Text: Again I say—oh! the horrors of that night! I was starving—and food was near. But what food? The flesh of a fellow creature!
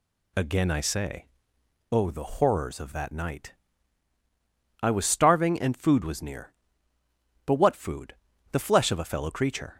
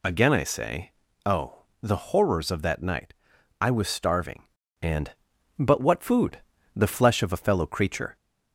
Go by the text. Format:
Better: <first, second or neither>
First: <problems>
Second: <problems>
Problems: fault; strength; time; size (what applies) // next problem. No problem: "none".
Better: first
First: none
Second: skips "food was near"; at 5.3 s